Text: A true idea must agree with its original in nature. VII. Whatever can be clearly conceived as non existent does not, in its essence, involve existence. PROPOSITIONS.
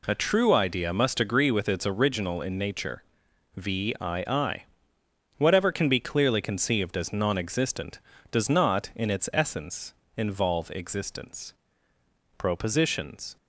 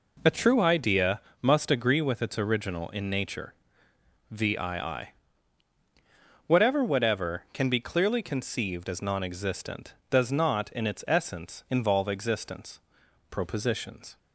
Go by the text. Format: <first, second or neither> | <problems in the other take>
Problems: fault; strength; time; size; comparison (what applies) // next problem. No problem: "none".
first | pauses between "idea" and "must"; slight; at 1.1 s; 0.22 s long // says "Whatever" twice; at 6.8 s